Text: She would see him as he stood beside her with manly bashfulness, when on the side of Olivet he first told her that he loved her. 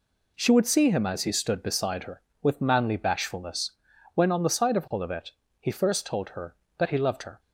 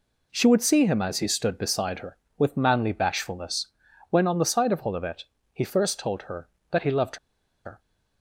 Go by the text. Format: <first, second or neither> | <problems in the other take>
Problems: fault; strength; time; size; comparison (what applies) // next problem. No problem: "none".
first | pauses between "Olivet" and "he"; slight; at 5.2 s; 0.28 s long; slight in the first // pauses between "loved" and "her"; noticeable; at 7.1 s; 0.48 s long